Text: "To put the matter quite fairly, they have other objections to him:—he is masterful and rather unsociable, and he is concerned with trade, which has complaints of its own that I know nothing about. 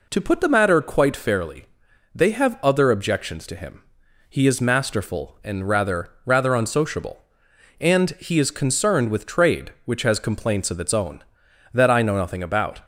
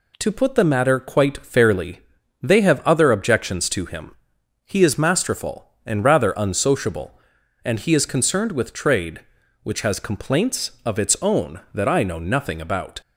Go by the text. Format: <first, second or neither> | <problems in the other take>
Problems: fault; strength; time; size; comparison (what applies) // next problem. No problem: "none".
second | says "rather" twice; at 6.2 s